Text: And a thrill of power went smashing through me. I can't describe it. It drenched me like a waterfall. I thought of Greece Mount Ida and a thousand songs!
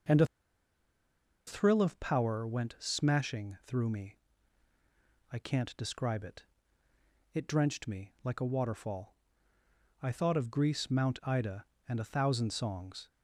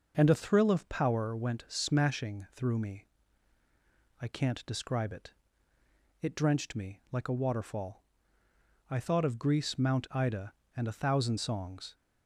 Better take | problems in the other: second | pauses between "a" and "thrill"; at 0.2 s; 1.2 s long

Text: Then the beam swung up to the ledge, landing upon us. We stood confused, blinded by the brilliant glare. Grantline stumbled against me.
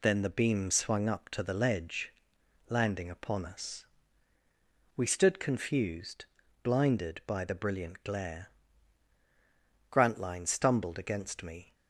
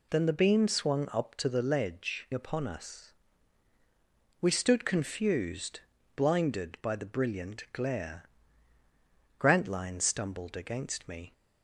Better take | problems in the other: first | skips "landing"; at 2.3 s

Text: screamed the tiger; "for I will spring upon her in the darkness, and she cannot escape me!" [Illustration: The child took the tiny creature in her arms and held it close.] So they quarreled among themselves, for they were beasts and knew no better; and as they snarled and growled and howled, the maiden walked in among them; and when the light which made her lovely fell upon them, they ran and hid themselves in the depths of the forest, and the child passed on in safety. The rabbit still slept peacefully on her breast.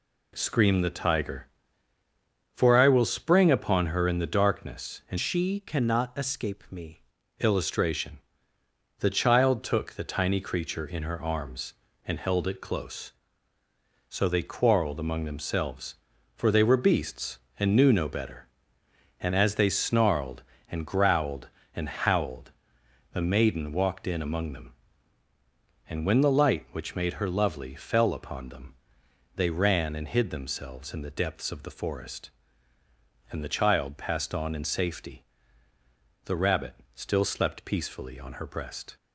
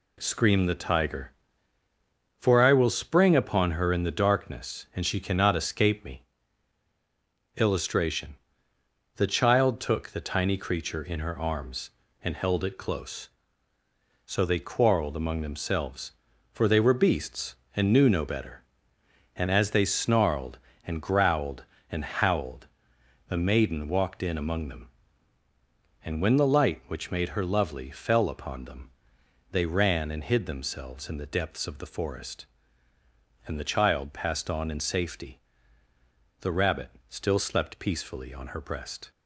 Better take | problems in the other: second | changes voice from "she" to "me"; from 5.1 to 7.0 s; 1.9 s long // pauses between "rabbit" and "still"; slight; at 36.7 s; 0.20 s long; slight in the second

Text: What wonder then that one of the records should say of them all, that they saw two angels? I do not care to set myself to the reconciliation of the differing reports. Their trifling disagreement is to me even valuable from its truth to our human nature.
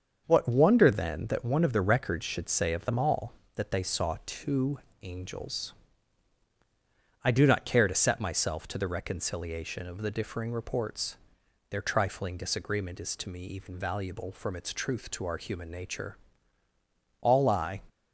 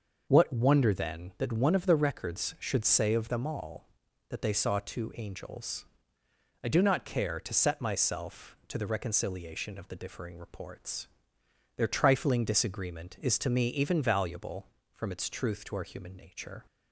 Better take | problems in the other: second | starts louder than the rest; until 1.2 s; 6.5 dB // pauses between "two" and "angels"; slight; at 4.7 s; 0.24 s long // goes on to say "All I"; noticeable; from 17.1 s on; 0.64 s long

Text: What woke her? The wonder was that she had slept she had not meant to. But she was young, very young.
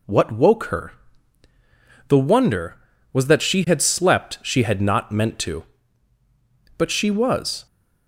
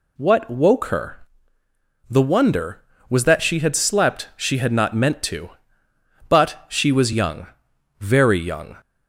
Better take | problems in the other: second | stops before "young very young"; at 7.6 s

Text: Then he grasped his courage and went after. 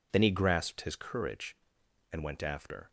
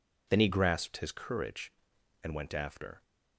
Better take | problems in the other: neither | none

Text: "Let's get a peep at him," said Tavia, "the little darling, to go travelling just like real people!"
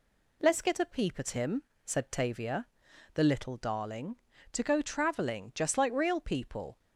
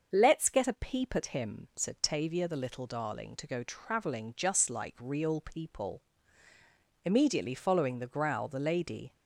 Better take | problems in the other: first | starts louder than the rest; until 1.1 s; 6.5 dB // goes on to say "Immediately following the growl the lady"; strong; from 7.0 s on; 2.0 s long

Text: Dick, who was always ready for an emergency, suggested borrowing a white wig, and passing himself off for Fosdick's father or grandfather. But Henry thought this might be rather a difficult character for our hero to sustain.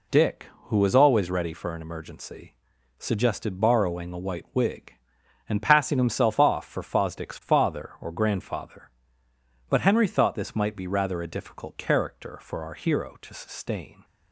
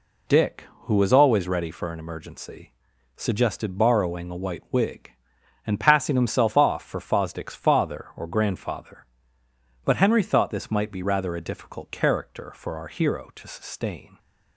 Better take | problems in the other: neither | none

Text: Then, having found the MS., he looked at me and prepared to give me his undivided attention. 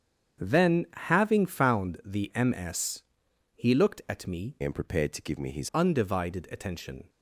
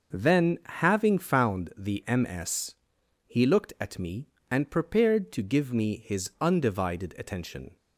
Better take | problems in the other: second | starts louder than the rest; strong; until 1.4 s; 8 dB // changes voice from "and" to "his"; from 4.6 to 5.6 s; 1.0 s long

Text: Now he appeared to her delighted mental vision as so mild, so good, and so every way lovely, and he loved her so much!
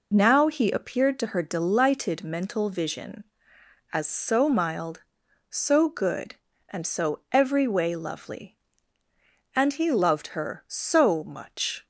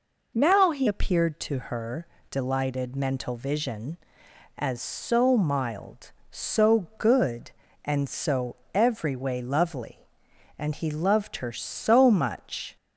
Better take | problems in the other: first | changes voice at "appeared"; from 0.8 s on; 11.9 s long // pauses between "her" and "delighted"; slight; at 2.0 s; 0.24 s long // pauses between "so" and "every"; slight; at 8.5 s; 0.18 s long

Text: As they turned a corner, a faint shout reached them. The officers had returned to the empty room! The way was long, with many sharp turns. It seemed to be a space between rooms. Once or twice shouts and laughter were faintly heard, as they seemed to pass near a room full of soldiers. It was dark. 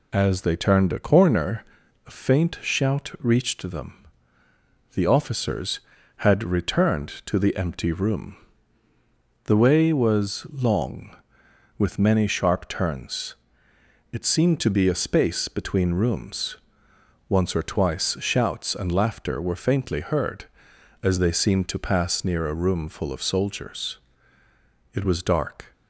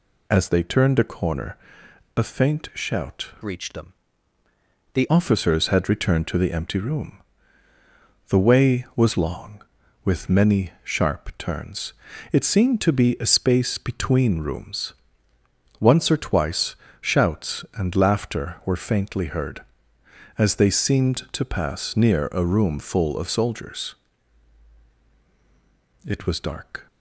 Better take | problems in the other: first | changes voice from "reached" to "The"; from 3.4 to 5.0 s; 1.6 s long // pauses between "twice" and "shouts"; slight; at 16.7 s; 0.26 s long

